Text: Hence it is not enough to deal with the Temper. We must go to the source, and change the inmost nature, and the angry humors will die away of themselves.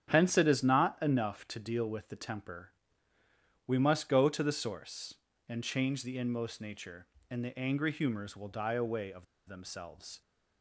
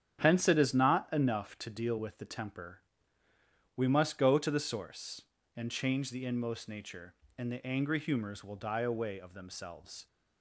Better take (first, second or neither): second